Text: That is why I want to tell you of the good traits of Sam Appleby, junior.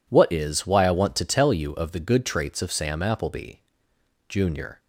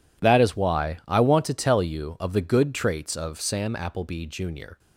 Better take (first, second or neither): second